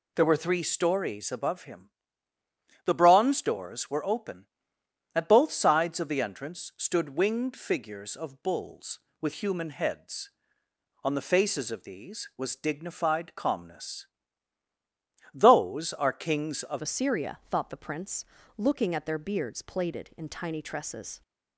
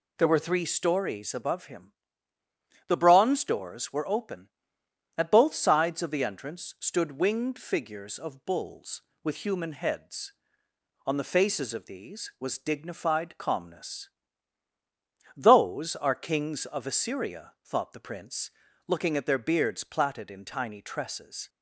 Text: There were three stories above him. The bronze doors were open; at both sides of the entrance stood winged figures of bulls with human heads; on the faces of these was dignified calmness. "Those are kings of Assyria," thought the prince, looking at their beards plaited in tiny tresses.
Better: second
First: changes voice at "Assyria"; from 16.8 s on; 4.4 s long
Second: none

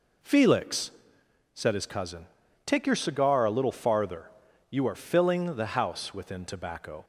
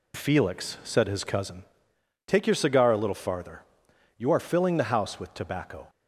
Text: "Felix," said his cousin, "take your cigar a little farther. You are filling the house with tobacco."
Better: second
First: says "within" for "with"; at 6.1 s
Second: none

